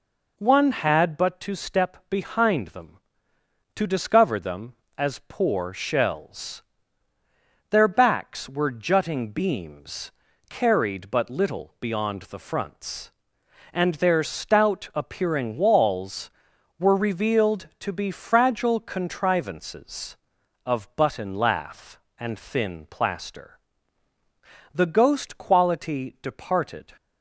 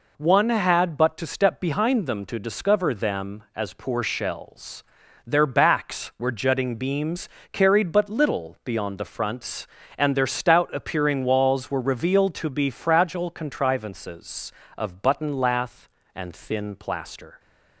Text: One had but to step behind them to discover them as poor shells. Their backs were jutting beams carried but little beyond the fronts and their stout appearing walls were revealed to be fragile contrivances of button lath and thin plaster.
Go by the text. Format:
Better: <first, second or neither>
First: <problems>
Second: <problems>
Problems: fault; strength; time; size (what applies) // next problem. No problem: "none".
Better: second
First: pauses between "beams" and "carried"; slight; at 10.1 s; 0.36 s long // goes on to say "The ghost quality departed"; strong; from 24.7 s on; 2.2 s long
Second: pauses between "beams" and "carried"; slight; at 7.2 s; 0.24 s long